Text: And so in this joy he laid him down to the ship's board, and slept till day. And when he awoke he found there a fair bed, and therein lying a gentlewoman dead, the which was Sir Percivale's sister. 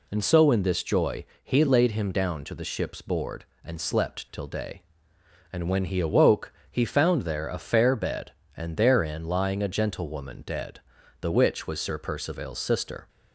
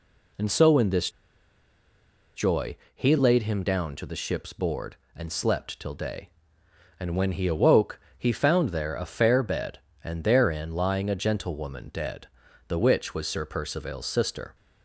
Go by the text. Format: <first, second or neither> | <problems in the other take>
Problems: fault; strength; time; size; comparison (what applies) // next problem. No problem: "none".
first | pauses between "this" and "joy"; strong; at 1.1 s; 1.2 s long // pauses between "joy" and "he"; slight; at 2.7 s; 0.18 s long; slight in the first // pauses between "awoke" and "he"; slight; at 7.9 s; 0.18 s long; slight in the first